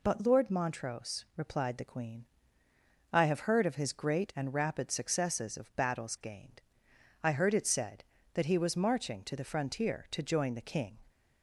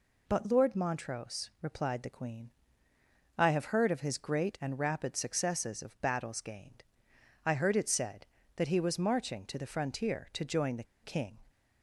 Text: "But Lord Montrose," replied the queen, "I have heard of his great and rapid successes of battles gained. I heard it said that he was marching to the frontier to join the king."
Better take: first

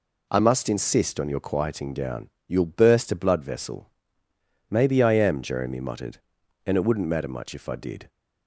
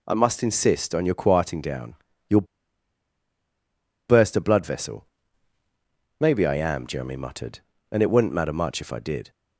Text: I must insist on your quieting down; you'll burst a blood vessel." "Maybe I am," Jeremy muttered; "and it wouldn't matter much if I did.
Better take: first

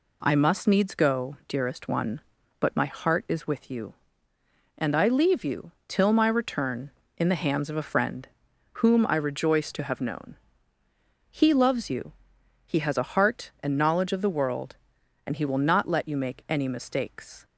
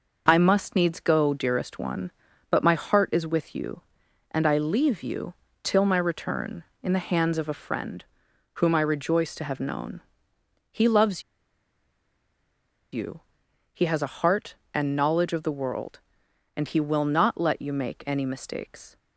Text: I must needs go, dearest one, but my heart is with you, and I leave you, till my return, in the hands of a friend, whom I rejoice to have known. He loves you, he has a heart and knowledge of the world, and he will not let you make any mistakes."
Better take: first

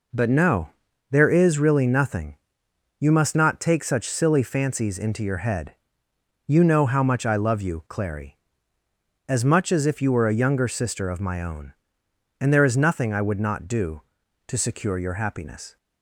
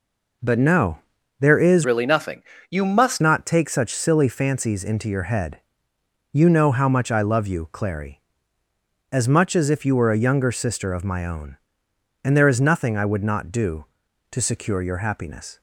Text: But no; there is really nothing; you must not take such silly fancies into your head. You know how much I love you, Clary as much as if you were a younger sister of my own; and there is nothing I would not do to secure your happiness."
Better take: first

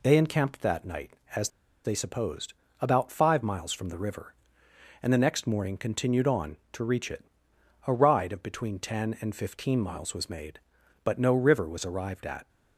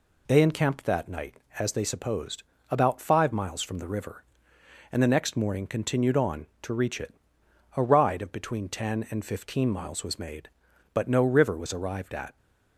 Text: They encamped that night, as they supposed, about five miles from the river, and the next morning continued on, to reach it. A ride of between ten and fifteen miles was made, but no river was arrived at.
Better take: second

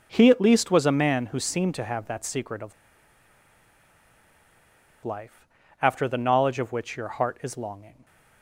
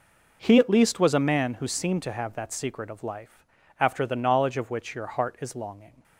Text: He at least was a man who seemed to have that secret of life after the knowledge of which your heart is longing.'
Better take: second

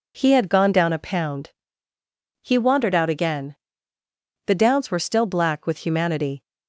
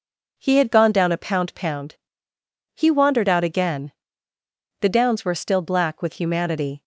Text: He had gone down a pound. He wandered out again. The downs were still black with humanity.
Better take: first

